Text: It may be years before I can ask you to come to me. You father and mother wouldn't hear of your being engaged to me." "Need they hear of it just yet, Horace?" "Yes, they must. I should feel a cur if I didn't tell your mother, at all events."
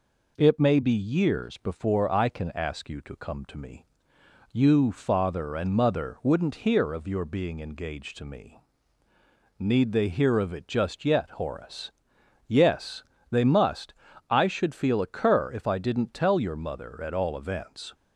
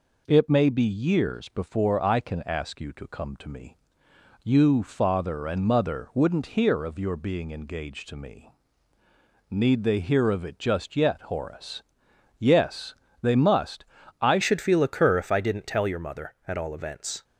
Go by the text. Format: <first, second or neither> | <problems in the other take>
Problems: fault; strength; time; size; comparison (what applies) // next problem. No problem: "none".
first | changes voice at "should"; from 14.4 s on; 2.8 s long